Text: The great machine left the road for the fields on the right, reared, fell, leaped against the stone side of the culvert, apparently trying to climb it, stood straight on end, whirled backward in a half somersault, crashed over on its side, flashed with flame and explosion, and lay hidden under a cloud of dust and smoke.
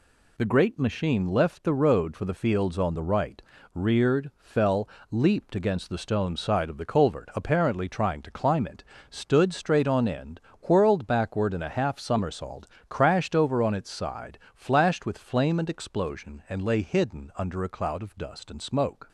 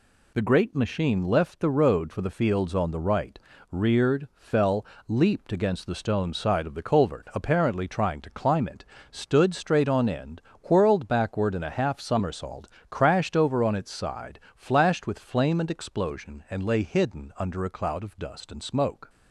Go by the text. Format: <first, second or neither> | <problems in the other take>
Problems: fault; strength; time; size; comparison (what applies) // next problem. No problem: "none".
neither | none